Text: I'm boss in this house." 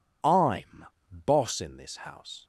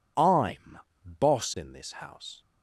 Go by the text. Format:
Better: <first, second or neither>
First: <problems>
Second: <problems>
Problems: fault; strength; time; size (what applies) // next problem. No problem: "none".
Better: neither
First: pauses between "I'm" and "boss"; at 0.8 s; 0.39 s long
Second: pauses between "I'm" and "boss"; at 0.7 s; 0.40 s long